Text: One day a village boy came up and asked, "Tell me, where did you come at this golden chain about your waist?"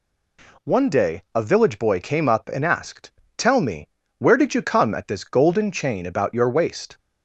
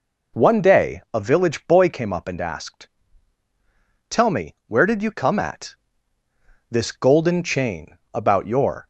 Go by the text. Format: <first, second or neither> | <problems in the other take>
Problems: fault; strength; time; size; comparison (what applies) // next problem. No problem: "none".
first | pauses between "at" and "this"; noticeable; at 5.7 s; 0.96 s long // pauses between "chain" and "about"; slight; at 7.9 s; 0.16 s long // stops before "waist"; at 8.8 s